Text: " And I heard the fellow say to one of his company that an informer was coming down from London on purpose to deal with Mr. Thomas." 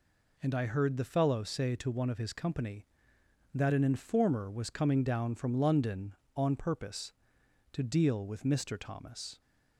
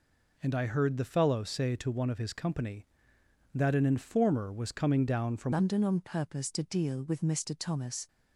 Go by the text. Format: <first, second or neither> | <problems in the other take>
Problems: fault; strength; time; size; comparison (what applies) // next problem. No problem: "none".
first | changes voice at "London"; from 5.5 s on; 2.5 s long